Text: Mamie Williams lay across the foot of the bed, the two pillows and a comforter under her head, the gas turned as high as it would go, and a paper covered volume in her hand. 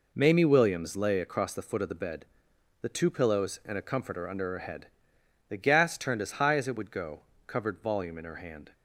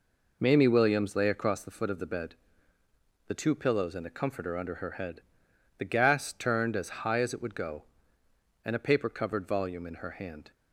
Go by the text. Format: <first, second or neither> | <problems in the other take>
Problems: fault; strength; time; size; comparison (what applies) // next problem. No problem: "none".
second | skips "and a paper"; at 7.3 s